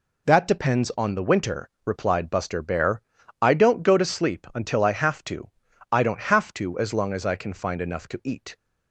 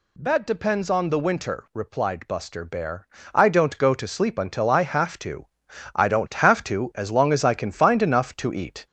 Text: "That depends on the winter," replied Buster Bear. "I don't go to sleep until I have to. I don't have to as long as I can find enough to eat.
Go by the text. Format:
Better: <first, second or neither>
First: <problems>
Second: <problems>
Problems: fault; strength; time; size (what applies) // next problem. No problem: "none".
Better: first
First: none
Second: gets louder; slight; throughout; 2.5 dB